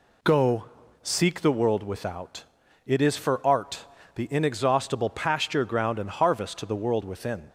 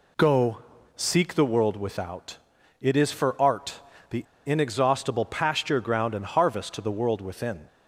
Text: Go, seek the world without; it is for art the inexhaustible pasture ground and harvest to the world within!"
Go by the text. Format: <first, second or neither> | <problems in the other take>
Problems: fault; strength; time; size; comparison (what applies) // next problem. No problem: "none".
first | pauses between "art" and "the"; slight; at 3.8 s; 0.30 s long; slight in the first // pauses between "the" and "inexhaustible"; slight; at 4.2 s; 0.24 s long